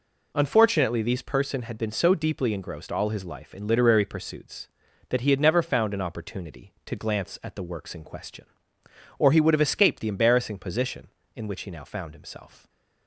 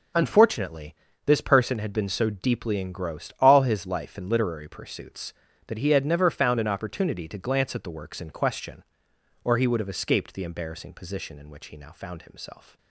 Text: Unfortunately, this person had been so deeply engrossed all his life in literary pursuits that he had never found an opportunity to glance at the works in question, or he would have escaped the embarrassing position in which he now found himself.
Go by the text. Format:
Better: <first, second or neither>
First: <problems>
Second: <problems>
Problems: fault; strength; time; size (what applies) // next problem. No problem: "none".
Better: second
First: says "these" for "this"; at 1.0 s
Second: none